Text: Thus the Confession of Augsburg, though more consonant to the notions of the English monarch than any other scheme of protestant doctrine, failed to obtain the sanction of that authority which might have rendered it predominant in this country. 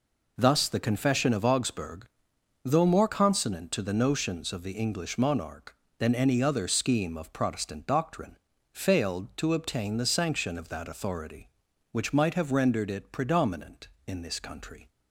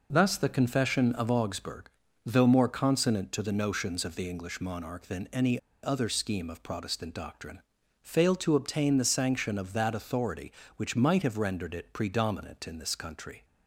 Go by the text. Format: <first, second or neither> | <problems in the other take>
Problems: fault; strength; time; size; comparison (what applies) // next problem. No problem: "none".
first | pauses between "any" and "other"; slight; at 5.5 s; 0.26 s long